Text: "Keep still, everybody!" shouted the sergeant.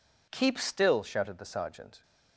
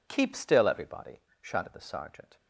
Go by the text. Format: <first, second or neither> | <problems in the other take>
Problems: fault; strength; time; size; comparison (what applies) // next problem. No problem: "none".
second | skips "everybody"; at 1.0 s